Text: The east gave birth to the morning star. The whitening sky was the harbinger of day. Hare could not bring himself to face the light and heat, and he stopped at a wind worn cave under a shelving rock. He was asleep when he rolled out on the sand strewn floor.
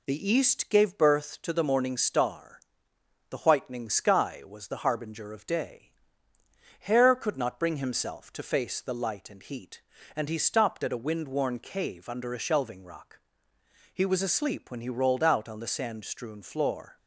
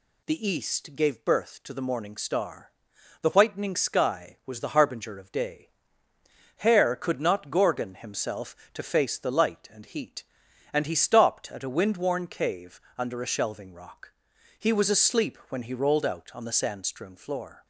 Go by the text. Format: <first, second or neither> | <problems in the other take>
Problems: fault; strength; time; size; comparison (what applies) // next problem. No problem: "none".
first | says "gorgon" for "bring"; at 7.5 s // pauses between "cave" and "under"; slight; at 12.7 s; 0.18 s long